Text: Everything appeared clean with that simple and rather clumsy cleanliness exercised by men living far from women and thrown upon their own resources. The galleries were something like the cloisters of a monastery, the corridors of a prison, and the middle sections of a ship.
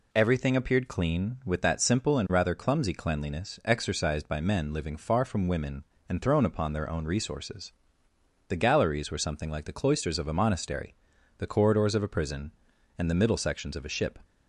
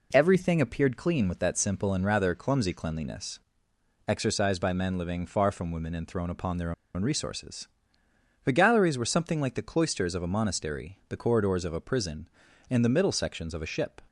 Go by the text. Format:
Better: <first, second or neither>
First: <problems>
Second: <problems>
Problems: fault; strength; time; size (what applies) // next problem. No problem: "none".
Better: first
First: none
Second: pauses between "cleanliness" and "exercised"; noticeable; at 3.3 s; 0.68 s long // pauses between "their" and "own"; slight; at 6.7 s; 0.23 s long